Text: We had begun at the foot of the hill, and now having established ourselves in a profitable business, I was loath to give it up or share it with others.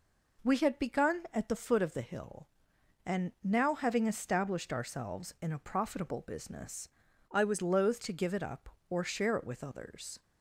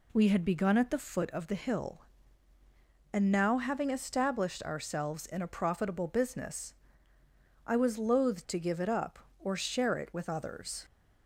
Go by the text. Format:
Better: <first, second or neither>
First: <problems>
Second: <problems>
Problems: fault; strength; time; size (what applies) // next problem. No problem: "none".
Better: second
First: changes voice from "I" to "was"; from 7.3 to 7.6 s; 0.3 s long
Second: none